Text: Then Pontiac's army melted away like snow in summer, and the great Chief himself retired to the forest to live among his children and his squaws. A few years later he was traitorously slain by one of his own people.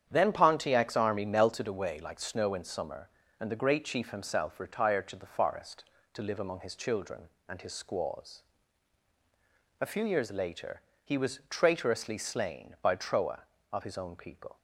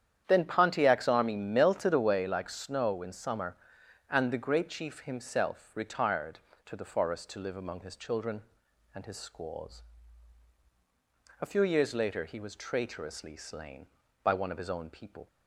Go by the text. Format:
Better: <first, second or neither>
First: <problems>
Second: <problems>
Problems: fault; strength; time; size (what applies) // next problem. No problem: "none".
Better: second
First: starts louder than the rest; strong; until 1.1 s; 9 dB // pauses between "later" and "he"; slight; at 10.8 s; 0.22 s long // says "troa" for "one"; at 12.9 s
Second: starts louder than the rest; strong; until 1.2 s; 9.5 dB